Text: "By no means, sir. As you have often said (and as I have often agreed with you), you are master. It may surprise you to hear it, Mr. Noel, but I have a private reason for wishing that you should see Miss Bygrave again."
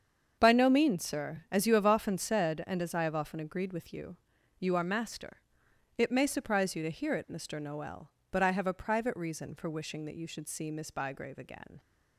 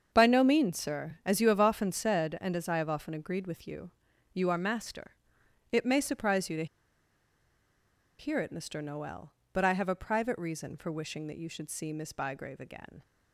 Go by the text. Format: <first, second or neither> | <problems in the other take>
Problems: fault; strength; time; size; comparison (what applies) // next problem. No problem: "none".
first | starts louder than the rest; until 1.1 s; 7 dB; also in the first // pauses between "to" and "hear"; strong; at 6.6 s; 1.5 s long